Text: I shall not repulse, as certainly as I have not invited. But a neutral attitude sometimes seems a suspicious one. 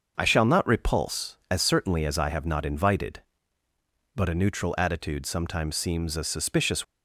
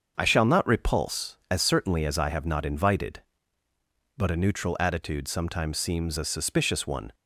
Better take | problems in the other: second | starts louder than the rest; until 1.1 s; 6.5 dB; also in the second // stops before "one"; at 6.8 s

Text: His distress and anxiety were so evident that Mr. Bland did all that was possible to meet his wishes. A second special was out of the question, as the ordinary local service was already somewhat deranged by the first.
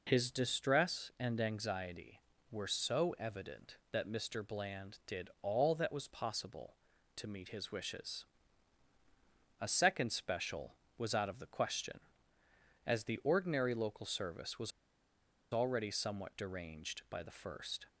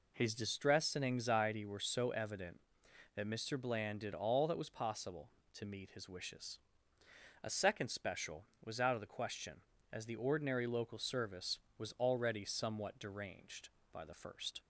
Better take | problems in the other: second | pauses between "was" and "already"; noticeable; at 14.7 s; 0.81 s long

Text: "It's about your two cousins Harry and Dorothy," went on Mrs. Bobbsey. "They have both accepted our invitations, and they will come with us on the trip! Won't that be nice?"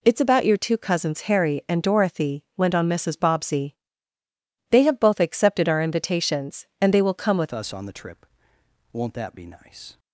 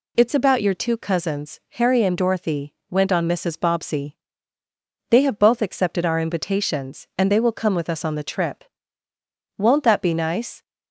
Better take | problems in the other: second | changes voice at "us"; from 7.5 s on; 2.4 s long

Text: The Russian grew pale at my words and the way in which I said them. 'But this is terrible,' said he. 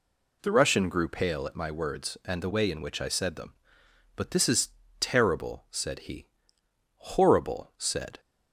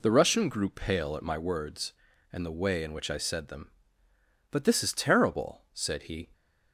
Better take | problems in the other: second | pauses between "is" and "terrible"; slight; at 4.6 s; 0.32 s long // goes on to say "Horrible said"; noticeable; from 6.9 s on; 1.2 s long

